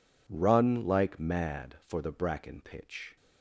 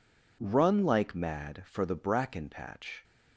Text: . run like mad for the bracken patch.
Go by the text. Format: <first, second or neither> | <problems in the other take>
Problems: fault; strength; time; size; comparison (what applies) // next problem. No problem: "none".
second | says "pitch" for "patch"; at 2.5 s